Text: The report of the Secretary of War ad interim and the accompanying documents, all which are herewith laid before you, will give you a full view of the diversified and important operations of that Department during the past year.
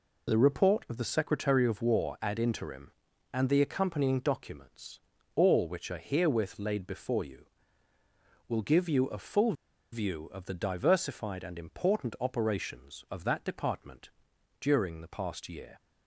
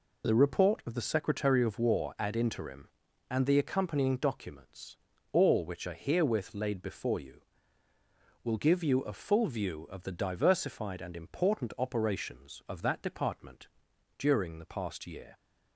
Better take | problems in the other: second | pauses between "full" and "view"; at 9.5 s; 0.39 s long // pauses between "Department" and "during"; noticeable; at 14.0 s; 0.50 s long; noticeable in the second

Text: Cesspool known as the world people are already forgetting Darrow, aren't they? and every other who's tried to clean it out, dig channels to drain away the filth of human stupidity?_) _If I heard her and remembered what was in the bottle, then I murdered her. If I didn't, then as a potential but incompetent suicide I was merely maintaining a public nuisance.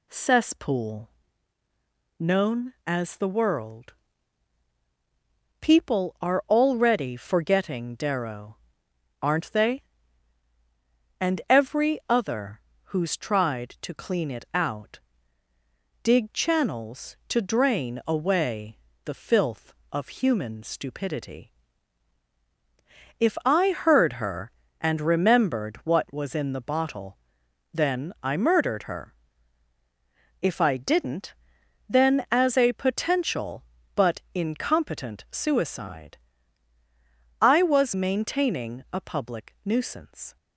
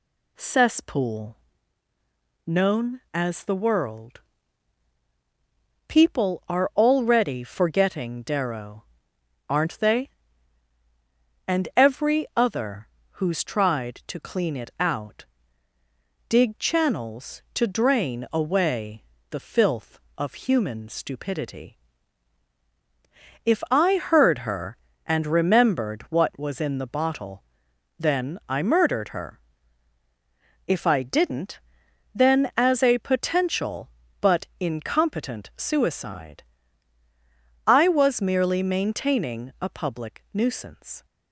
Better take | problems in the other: second | pauses between "Cesspool" and "known"; at 1.0 s; 1.1 s long; also in the second // pauses between "world" and "people"; strong; at 3.9 s; 1.6 s long; strong in the second // pauses between "other" and "who's"; slight; at 12.5 s; 0.26 s long; slight in the second // pauses between "away" and "the"; slight; at 18.7 s; 0.26 s long; slight in the second // pauses between "suicide" and "I"; strong; at 36.1 s; 1.2 s long; strong in the second // skips "merely"; at 37.9 s

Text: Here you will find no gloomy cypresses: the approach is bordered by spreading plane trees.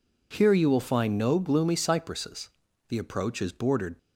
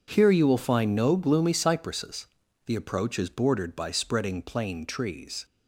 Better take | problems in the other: second | stops before "by spreading plane trees"; at 3.9 s

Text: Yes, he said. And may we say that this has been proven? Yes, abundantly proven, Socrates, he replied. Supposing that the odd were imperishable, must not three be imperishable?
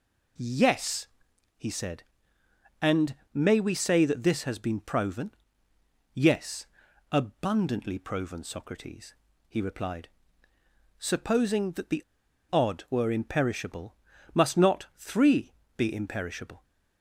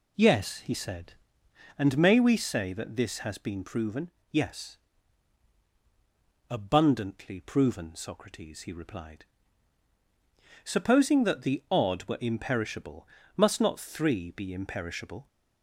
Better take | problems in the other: second | pauses between "And" and "may"; slight; at 3.1 s; 0.18 s long // pauses between "the" and "odd"; noticeable; at 12.0 s; 0.48 s long // pauses between "three" and "be"; slight; at 15.5 s; 0.24 s long

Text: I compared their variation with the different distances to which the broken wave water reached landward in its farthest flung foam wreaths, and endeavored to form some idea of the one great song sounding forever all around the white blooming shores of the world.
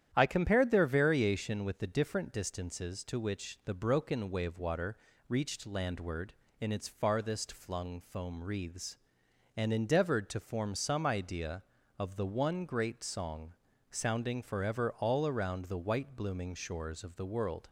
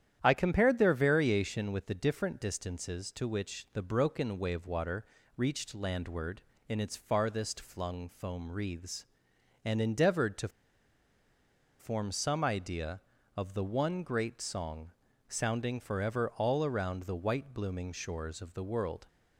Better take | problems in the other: first | starts louder than the rest; strong; until 1.2 s; 10 dB; strong in the first // pauses between "water" and "reached"; slight; at 5.0 s; 0.28 s long; slight in the first // pauses between "to" and "form"; strong; at 10.4 s; 1.3 s long // pauses between "song" and "sounding"; slight; at 14.9 s; 0.36 s long; slight in the first

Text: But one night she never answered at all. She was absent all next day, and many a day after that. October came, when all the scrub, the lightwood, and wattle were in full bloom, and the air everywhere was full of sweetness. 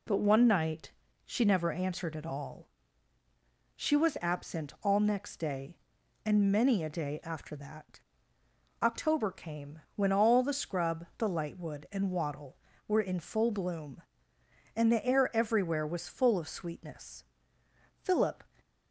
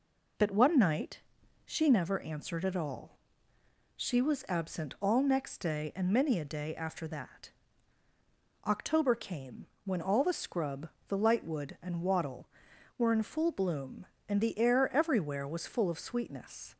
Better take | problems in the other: second | pauses between "night" and "she"; slight; at 0.9 s; 0.34 s long; also in the second // goes on to say "Philip"; slight; from 18.0 s on; 0.40 s long

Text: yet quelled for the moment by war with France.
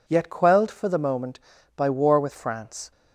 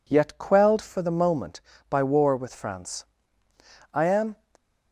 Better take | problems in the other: first | goes on to say "I am"; slight; from 3.9 s on; 0.46 s long

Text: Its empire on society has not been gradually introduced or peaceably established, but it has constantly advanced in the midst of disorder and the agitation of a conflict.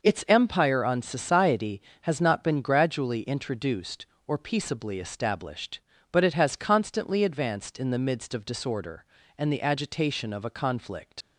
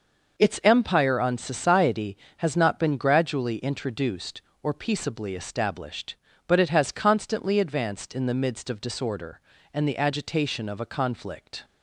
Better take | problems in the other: second | leaves "conflict" unfinished; at 11.2 s; 80 ms

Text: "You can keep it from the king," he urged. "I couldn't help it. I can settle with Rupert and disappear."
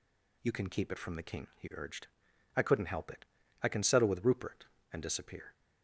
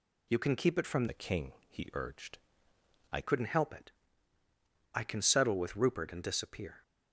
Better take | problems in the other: first | changes voice from "the" to "I"; from 1.0 to 3.2 s; 2.2 s long

